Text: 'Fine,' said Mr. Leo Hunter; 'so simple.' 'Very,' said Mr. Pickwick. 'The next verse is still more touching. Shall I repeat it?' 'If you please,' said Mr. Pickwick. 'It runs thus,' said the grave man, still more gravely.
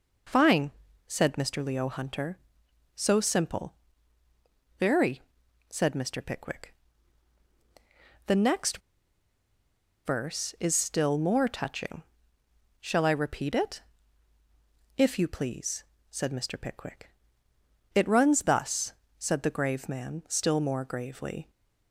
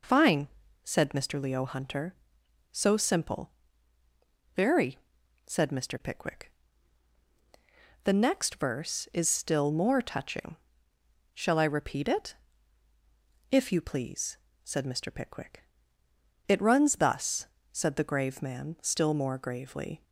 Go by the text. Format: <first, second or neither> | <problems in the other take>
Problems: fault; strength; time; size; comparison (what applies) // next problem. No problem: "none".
second | pauses between "next" and "verse"; strong; at 8.8 s; 1.2 s long